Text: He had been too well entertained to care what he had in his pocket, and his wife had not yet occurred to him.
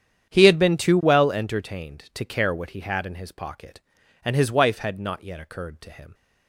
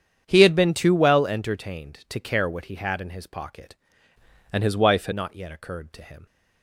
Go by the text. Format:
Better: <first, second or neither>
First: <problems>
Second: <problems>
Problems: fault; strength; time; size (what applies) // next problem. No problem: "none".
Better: first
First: starts louder than the rest; strong; until 1.3 s; 9 dB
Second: starts louder than the rest; strong; until 1.2 s; 8.5 dB // changes voice from "and" to "had"; from 4.5 to 5.1 s; 0.6 s long